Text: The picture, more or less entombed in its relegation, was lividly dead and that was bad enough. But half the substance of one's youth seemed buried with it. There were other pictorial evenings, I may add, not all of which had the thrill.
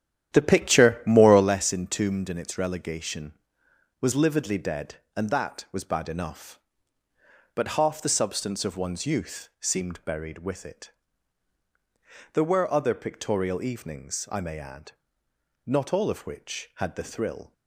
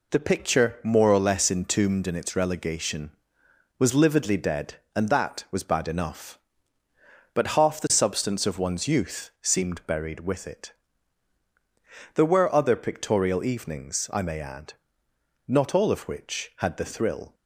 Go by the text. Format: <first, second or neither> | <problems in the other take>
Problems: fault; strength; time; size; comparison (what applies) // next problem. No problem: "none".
second | starts louder than the rest; strong; until 1.6 s; 11 dB